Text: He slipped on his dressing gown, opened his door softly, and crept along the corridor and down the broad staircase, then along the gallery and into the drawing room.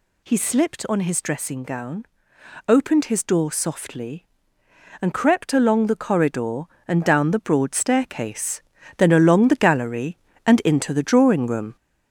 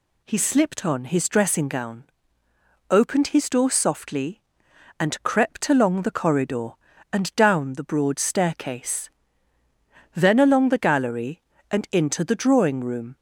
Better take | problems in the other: second | gets louder; noticeable; throughout; 5 dB

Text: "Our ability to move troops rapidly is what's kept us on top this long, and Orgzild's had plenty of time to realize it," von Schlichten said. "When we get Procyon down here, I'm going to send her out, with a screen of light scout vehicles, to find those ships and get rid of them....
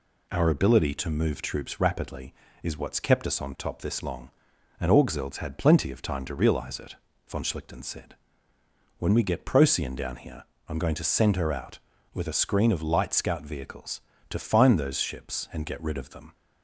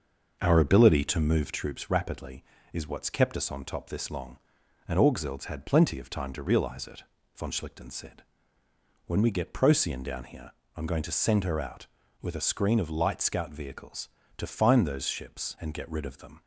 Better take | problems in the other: first | starts louder than the rest; noticeable; until 1.7 s; 6 dB

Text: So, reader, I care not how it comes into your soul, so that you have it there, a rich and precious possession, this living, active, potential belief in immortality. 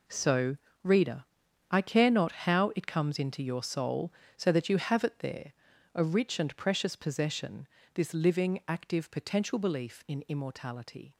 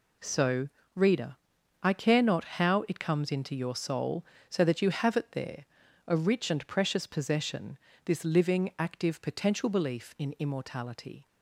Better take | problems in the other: second | gets quieter; strong; throughout; 12.5 dB

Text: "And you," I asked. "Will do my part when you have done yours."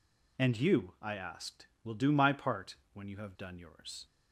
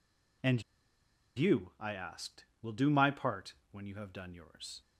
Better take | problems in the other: first | pauses between "And" and "you"; noticeable; at 0.6 s; 0.73 s long // pauses between "part" and "when"; slight; at 3.5 s; 0.18 s long; slight in the first

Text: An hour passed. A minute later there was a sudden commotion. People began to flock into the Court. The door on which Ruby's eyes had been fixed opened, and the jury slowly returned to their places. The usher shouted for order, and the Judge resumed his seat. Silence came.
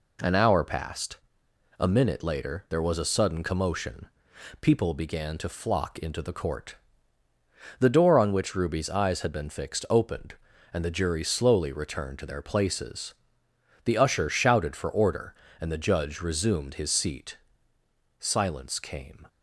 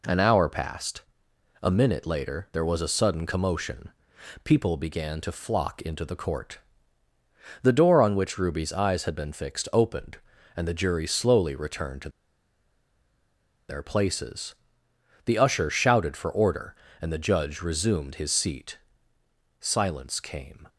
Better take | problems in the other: first | pauses between "to" and "their"; strong; at 12.0 s; 1.6 s long

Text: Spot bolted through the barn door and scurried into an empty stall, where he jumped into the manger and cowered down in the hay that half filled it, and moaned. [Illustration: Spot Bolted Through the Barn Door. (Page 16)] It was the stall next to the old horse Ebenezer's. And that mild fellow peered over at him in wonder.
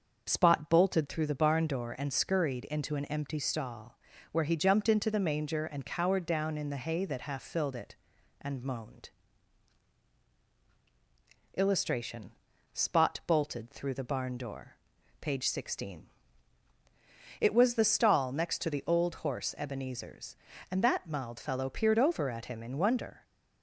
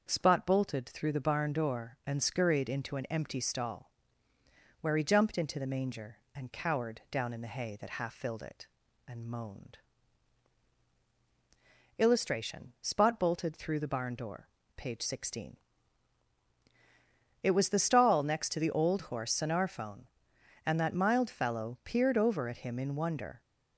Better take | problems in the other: first | starts louder than the rest; until 1.1 s; 6.5 dB; also in the first // says "Sonarphone" for "Ebenezer's"; at 19.3 s

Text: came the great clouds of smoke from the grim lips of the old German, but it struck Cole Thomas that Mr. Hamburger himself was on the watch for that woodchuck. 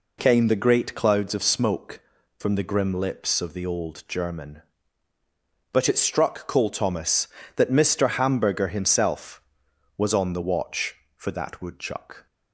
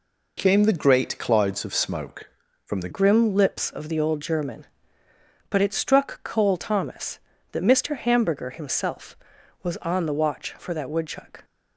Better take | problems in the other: first | changes voice at "grim"; from 2.9 s on; 8.5 s long

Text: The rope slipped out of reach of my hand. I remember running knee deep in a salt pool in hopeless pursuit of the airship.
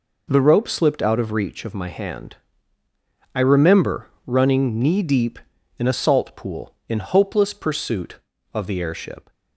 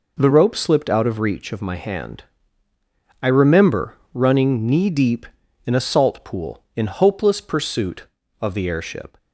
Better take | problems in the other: neither | pauses between "remember" and "running"; slight; the same in both

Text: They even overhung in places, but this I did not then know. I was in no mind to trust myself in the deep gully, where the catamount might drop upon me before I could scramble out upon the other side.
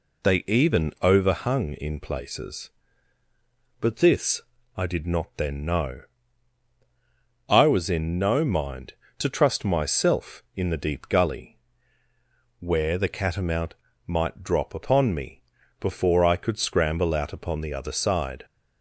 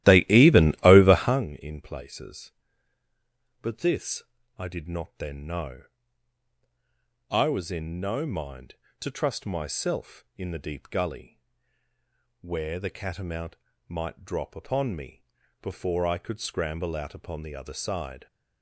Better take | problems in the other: first | starts louder than the rest; strong; until 1.5 s; 14.5 dB // pauses between "this" and "I"; slight; at 4.2 s; 0.36 s long; slight in the first // pauses between "catamount" and "might"; slight; at 13.5 s; 0.32 s long; slight in the first // pauses between "me" and "before"; at 15.2 s; 0.38 s long; also in the first

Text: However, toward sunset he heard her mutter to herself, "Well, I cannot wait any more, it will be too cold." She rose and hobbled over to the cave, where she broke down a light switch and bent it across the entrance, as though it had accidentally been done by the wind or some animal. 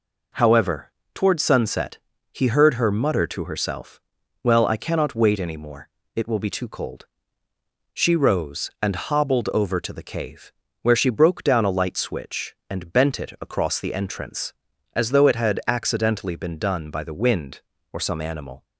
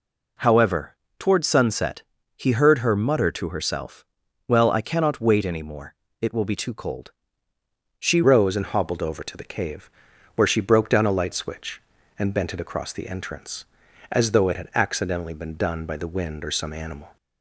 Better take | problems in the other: first | pauses between "sunset" and "he"; slight; at 2.0 s; 0.32 s long; slight in the first // changes voice at "rose"; from 8.2 s on; 8.9 s long

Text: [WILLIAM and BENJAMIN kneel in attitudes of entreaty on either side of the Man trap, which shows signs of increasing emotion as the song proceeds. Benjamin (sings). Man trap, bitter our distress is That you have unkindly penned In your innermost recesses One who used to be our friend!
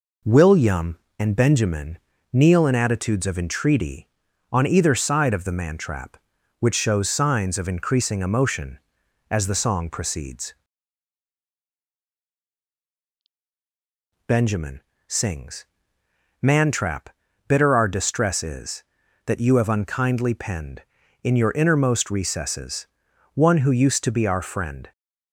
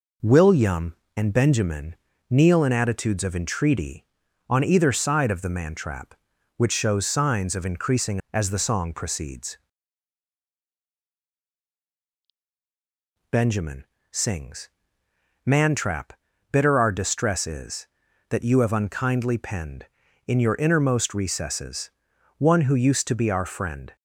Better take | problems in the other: first | pauses between "BENJAMIN" and "kneel"; slight; at 1.9 s; 0.34 s long; slight in the first // skips "emotion"; at 8.2 s // pauses between "recesses" and "One"; noticeable; at 21.8 s; 0.48 s long; noticeable in the first

